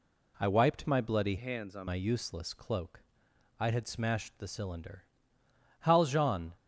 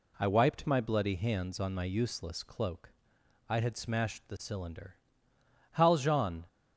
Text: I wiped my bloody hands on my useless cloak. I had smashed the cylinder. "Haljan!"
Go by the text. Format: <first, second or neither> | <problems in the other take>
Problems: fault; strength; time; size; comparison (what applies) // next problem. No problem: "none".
second | changes voice from "hands" to "on"; from 1.3 to 1.8 s; 0.5 s long